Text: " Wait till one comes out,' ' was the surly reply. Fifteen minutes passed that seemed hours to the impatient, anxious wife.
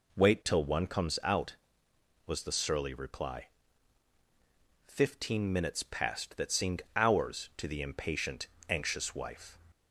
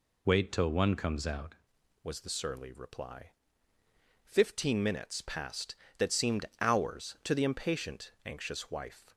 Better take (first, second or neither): first